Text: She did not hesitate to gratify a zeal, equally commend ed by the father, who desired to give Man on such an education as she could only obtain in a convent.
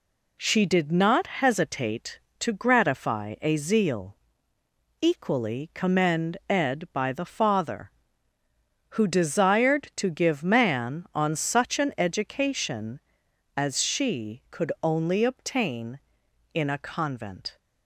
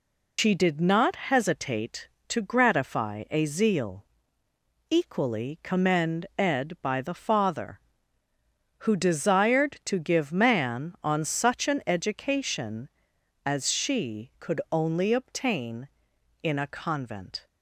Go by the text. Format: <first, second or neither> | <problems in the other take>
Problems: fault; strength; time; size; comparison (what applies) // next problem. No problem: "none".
first | loses the start of "She"; at 0.3 s; 100 ms